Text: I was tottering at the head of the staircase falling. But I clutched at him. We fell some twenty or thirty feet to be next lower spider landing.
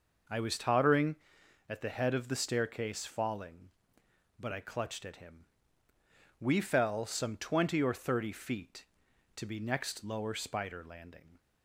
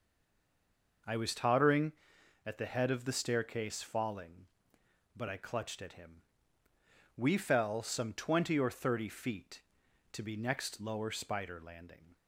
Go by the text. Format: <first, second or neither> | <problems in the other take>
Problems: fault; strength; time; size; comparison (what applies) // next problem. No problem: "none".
first | stays silent before the first word; until 1.0 s; 1.0 s long